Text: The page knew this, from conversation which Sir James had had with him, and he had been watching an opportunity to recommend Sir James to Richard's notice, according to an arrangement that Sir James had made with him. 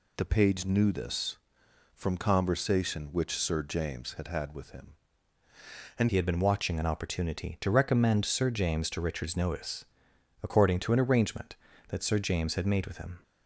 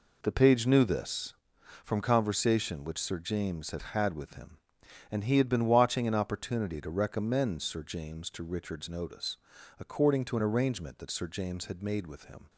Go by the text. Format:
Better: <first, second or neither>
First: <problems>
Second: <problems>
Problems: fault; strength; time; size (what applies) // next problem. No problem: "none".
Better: second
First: changes voice at "he"; from 6.0 s on; 7.2 s long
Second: none